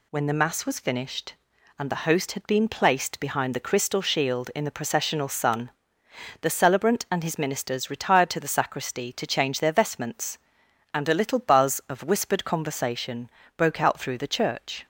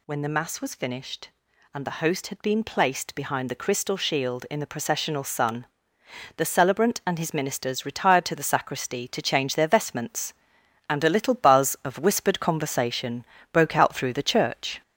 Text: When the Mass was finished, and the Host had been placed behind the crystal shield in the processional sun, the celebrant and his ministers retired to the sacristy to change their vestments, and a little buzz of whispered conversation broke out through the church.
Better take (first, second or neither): first